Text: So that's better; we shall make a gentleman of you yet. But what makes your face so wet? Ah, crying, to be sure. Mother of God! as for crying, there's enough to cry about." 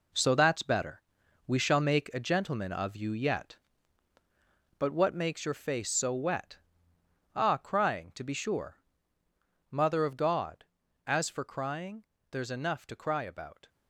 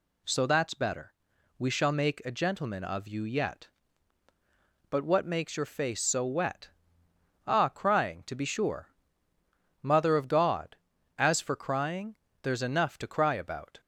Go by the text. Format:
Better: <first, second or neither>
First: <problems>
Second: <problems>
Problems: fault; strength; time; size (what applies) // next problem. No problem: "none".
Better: second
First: gets quieter; strong; throughout; 9 dB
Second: none